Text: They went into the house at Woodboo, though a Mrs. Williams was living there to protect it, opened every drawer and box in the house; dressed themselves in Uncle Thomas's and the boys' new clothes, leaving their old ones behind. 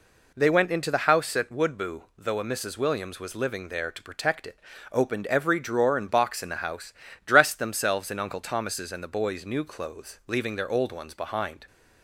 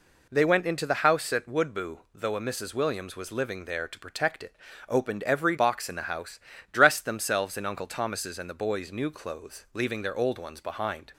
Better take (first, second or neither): first